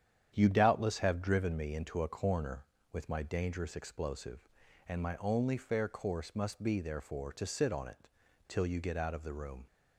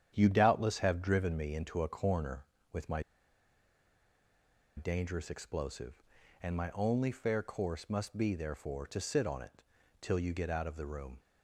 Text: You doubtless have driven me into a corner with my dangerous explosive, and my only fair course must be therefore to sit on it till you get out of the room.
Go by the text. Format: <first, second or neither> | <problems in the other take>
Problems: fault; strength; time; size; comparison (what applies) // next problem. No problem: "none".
first | starts louder than the rest; strong; until 1.1 s; 9 dB; strong in the first // pauses between "my" and "dangerous"; strong; at 3.0 s; 1.7 s long // pauses between "it" and "till"; at 9.6 s; 0.40 s long; also in the first